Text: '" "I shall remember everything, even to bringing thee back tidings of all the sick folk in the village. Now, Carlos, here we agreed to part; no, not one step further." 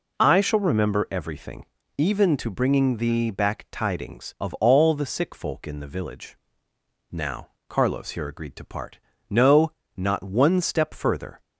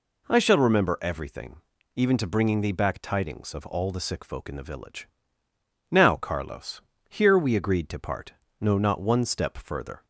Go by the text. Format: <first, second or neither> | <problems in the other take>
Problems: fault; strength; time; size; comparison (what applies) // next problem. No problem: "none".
second | skips "we"; at 8.2 s